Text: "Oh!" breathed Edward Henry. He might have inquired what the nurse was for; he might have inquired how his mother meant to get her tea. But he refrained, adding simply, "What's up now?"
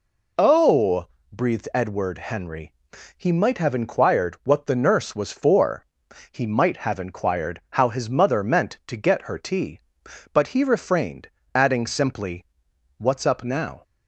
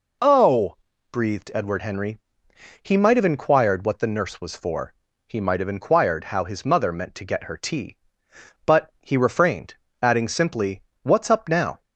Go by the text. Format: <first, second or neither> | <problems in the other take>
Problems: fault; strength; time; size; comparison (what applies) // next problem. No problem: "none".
neither | none